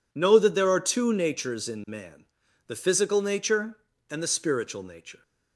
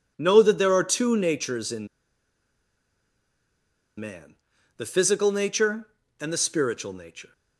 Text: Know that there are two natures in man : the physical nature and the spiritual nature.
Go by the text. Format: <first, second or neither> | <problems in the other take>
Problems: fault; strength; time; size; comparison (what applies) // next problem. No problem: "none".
first | pauses between "in" and "man"; strong; at 1.8 s; 2.1 s long